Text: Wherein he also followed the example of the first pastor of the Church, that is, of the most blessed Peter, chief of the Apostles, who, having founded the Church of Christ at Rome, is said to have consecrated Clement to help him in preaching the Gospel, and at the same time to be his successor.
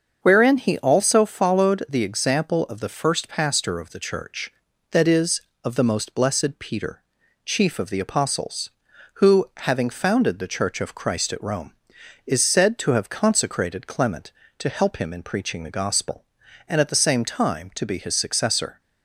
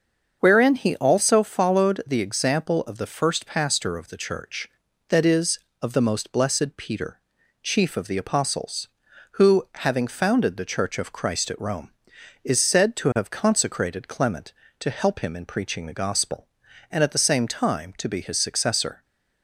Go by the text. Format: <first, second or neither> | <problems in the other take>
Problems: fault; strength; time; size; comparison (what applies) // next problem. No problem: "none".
neither | starts louder than the rest; the same in both